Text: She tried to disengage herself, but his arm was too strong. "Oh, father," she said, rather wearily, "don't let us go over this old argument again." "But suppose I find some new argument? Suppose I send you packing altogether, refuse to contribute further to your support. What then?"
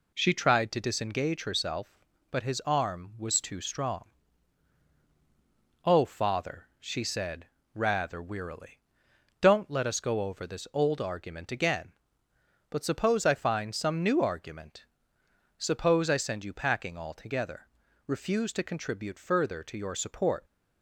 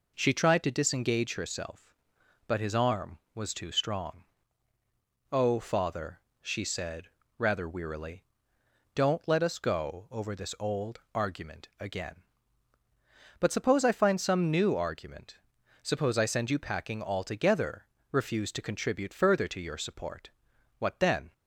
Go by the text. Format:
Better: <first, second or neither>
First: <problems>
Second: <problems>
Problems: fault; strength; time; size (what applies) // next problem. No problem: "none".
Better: second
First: stops before "What then"; at 20.4 s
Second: none